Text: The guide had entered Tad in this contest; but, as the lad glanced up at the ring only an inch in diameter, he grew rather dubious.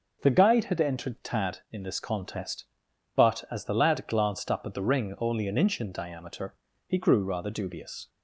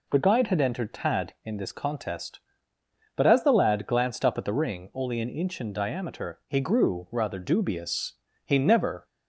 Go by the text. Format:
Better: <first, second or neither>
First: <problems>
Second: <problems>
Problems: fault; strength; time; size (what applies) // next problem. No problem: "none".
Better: first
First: none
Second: goes on to say "He never"; from 8.4 s on; 0.60 s long